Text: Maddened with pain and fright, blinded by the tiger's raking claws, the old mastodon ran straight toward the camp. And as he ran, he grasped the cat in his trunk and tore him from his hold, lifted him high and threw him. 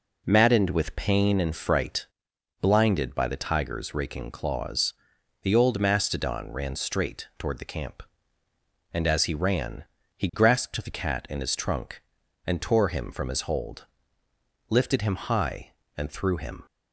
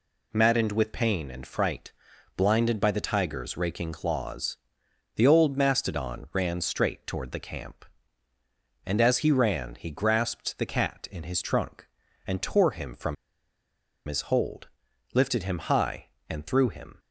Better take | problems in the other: first | pauses between "from" and "his"; noticeable; at 13.1 s; 0.91 s long

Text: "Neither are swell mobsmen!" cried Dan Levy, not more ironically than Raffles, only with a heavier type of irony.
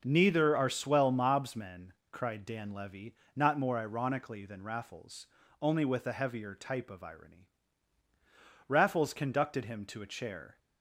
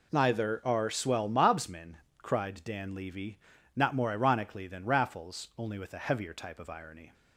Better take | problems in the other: second | goes on to say "Raffles conducted him to a chair"; strong; from 8.6 s on; 1.9 s long

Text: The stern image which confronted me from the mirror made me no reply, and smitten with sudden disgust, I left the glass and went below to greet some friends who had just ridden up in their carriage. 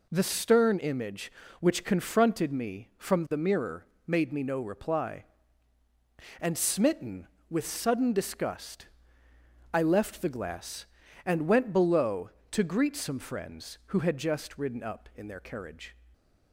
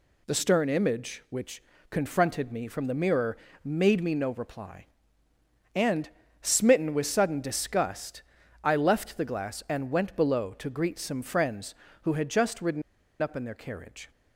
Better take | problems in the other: first | pauses between "which" and "confronted"; slight; at 1.6 s; 0.28 s long // pauses between "mirror" and "made"; slight; at 3.3 s; 0.28 s long; slight in the first // pauses between "and" and "smitten"; slight; at 6.0 s; 0.34 s long // pauses between "ridden" and "up"; at 12.8 s; 0.39 s long

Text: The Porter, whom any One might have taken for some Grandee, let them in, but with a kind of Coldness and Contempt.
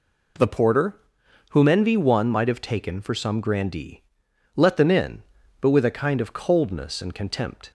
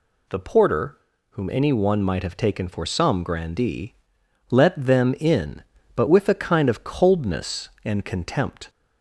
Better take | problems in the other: second | says "envy" for "any"; at 1.6 s

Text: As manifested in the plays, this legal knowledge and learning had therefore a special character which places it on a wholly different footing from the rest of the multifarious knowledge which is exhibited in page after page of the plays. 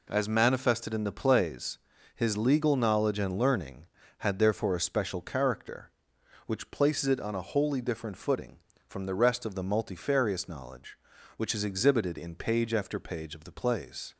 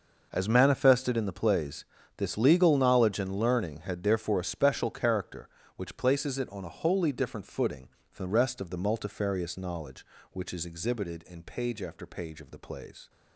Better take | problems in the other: second | says "his" for "this"; at 2.1 s

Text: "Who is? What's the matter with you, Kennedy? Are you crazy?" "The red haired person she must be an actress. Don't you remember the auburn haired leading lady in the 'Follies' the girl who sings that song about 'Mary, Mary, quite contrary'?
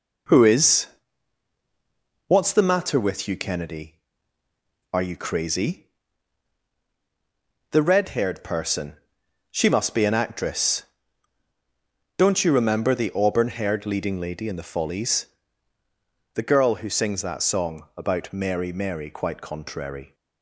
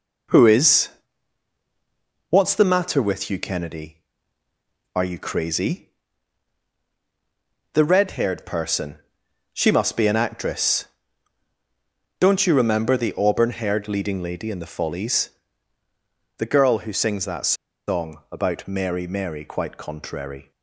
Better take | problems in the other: first | pauses between "person" and "she"; noticeable; at 8.9 s; 0.54 s long; noticeable in the first // pauses between "Follies" and "the"; at 15.2 s; 1.0 s long; also in the first // pauses between "that" and "song"; slight; at 17.5 s; 0.34 s long

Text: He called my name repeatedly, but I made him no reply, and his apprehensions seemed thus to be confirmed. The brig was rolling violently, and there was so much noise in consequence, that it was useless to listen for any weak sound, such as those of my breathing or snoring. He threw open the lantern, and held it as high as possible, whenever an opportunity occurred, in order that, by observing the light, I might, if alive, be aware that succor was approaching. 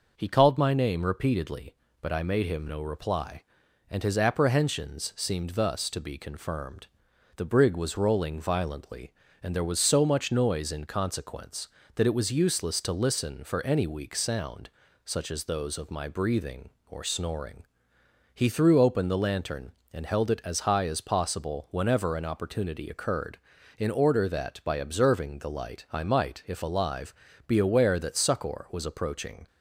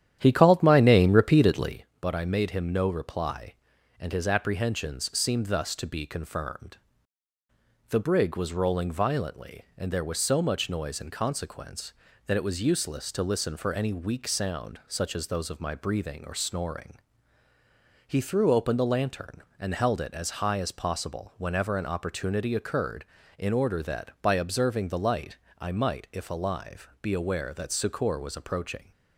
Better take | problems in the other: first | starts louder than the rest; strong; until 1.8 s; 10.5 dB

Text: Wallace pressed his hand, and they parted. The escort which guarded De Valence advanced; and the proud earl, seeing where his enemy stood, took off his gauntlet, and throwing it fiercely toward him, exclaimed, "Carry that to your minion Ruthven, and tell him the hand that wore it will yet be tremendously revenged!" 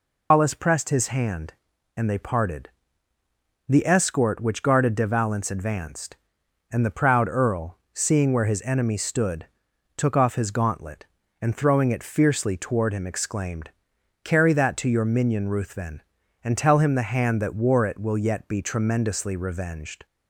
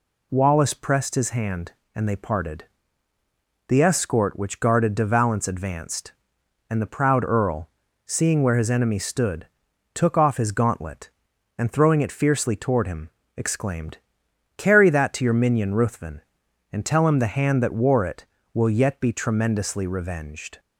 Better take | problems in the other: second | loses the start of "Wallace"; at 0.3 s; 150 ms

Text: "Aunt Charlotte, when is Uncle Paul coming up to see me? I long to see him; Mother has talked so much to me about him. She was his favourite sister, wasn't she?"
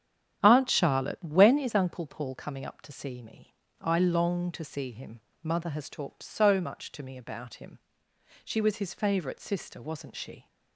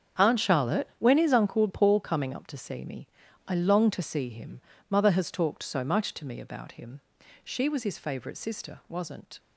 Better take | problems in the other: first | starts louder than the rest; strong; until 1.2 s; 8 dB; strong in the first // stops before "she"; at 9.3 s

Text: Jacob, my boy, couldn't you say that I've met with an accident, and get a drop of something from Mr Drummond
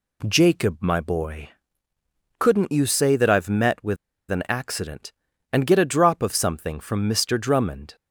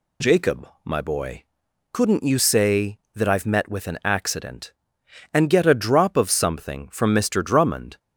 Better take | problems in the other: second | pauses between "with" and "an"; slight; at 3.9 s; 0.34 s long

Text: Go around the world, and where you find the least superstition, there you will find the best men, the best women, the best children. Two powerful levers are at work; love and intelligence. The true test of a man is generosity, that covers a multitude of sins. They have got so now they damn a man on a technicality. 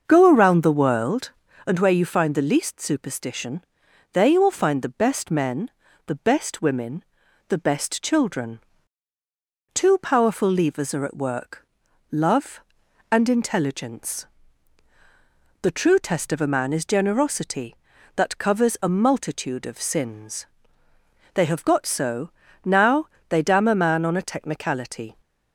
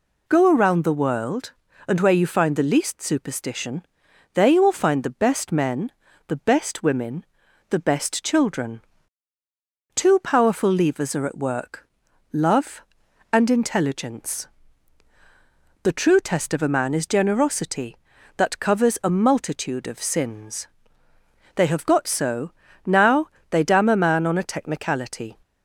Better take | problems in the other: second | starts louder than the rest; until 1.7 s; 6.5 dB // pauses between "so" and "now"; slight; at 22.2 s; 0.34 s long; slight in the second // pauses between "now" and "they"; slight; at 23.0 s; 0.22 s long; slight in the second

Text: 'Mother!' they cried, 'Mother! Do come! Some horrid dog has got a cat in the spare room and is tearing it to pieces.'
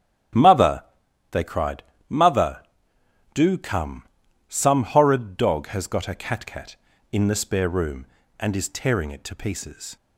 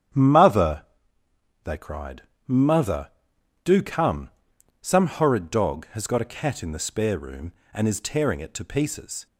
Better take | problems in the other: second | starts louder than the rest; strong; until 1.8 s; 10.5 dB; strong in the second // says "cat" twice; at 6.4 s

